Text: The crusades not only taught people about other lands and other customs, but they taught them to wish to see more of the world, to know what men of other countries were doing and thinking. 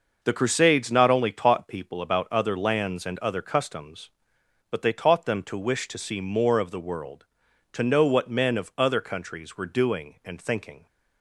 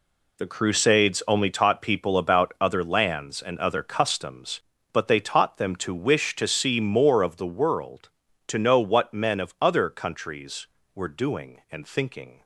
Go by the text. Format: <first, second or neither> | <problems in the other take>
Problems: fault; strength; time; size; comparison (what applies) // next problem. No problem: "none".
first | skips "not"; at 1.2 s